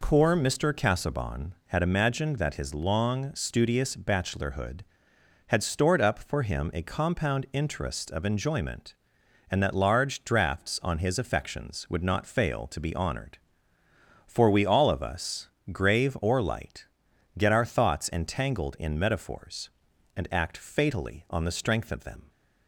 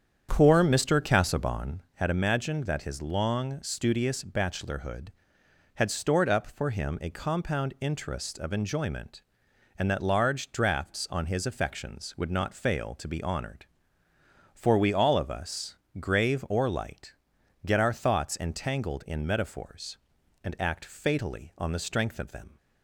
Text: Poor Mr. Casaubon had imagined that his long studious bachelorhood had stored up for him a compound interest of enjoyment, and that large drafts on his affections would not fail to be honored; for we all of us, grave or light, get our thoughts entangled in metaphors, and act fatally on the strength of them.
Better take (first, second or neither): first